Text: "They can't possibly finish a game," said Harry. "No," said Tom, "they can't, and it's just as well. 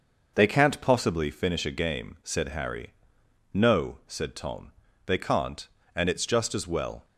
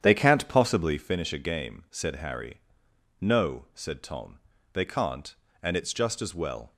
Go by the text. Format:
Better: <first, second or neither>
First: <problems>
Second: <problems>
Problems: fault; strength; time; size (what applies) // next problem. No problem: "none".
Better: first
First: none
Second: starts louder than the rest; strong; until 1.2 s; 9 dB